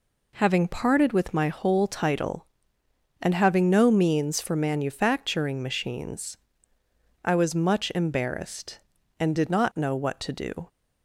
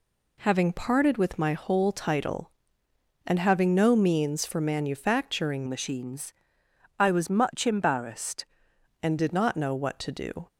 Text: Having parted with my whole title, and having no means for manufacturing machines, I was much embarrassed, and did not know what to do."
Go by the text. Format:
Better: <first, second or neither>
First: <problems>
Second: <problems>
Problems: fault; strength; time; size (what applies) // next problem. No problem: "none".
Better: first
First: none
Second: changes voice from "machines" to "embarrassed"; from 5.6 to 8.4 s; 2.8 s long